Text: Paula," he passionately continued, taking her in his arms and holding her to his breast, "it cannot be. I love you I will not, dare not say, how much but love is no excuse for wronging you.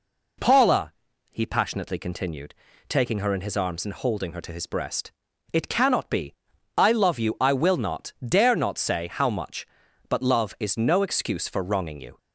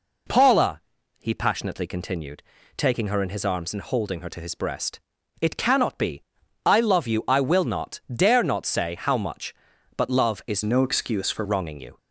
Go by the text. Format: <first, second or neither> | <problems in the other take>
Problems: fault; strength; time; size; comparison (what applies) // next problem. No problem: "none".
first | changes voice from "no" to "for"; from 10.6 to 11.4 s; 0.8 s long